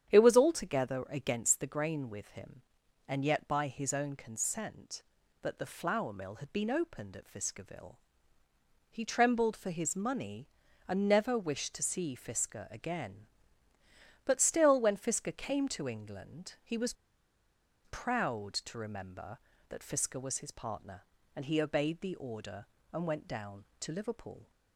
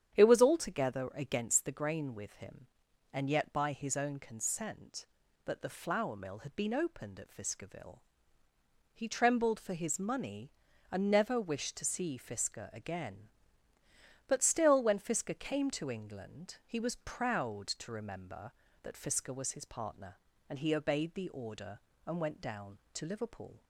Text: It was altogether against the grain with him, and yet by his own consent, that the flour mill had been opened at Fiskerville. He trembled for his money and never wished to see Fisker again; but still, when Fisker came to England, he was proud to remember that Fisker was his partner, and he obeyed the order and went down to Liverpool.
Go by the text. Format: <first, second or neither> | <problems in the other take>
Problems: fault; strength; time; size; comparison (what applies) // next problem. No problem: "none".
second | starts louder than the rest; strong; until 1.1 s; 9 dB; strong in the second // pauses between "was" and "proud"; noticeable; at 16.9 s; 0.91 s long